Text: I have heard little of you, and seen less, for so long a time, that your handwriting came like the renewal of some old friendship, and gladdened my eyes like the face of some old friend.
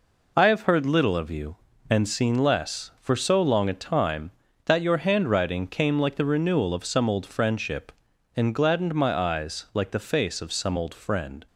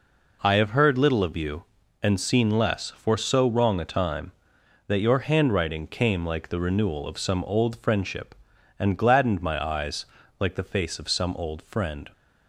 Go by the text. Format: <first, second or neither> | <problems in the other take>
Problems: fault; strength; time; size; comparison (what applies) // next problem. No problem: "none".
first | says "wrong" for "long"; at 3.4 s // pauses between "eyes" and "like"; slight; at 10.0 s; 0.34 s long